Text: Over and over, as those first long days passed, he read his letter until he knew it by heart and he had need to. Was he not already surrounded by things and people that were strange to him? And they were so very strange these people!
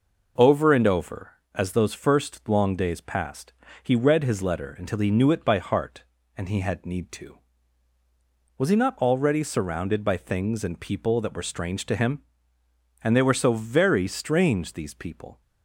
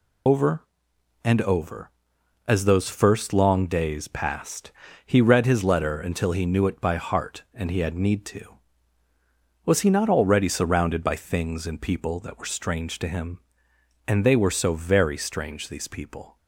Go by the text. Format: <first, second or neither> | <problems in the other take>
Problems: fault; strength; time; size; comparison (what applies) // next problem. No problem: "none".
first | loses the start of "Over"; at 0.2 s; 75 ms